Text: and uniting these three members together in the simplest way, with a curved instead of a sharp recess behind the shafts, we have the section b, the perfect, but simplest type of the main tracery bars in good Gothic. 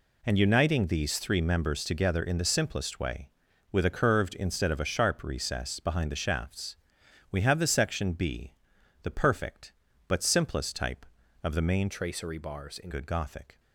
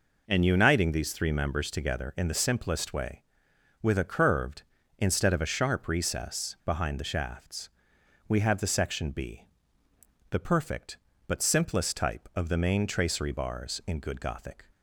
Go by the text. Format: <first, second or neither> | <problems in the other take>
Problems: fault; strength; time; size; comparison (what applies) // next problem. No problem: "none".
second | changes voice from "tracery" to "in"; from 11.9 to 12.8 s; 0.9 s long